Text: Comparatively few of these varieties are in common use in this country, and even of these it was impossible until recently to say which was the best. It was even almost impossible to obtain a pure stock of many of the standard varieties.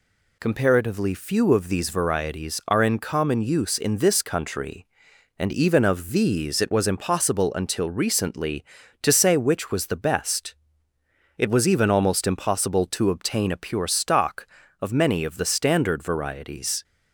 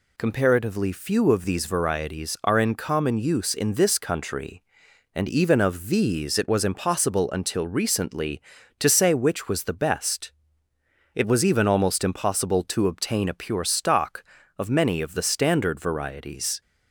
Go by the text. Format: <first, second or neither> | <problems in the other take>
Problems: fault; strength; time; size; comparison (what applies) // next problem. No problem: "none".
neither | none